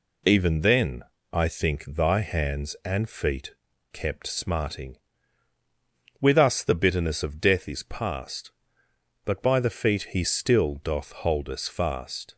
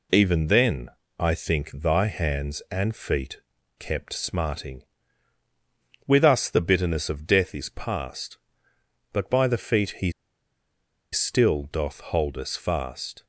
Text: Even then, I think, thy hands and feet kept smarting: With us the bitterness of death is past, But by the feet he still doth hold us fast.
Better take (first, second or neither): first